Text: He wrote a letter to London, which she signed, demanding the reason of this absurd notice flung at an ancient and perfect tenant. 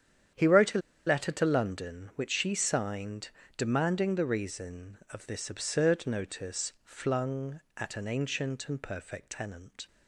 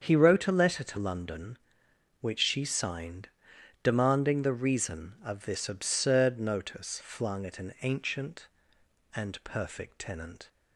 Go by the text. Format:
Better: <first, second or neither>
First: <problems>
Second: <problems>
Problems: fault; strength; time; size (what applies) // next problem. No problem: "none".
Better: second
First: starts louder than the rest; strong; until 1.6 s; 9 dB // pauses between "a" and "letter"; slight; at 0.7 s; 0.27 s long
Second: starts louder than the rest; strong; until 1.0 s; 7 dB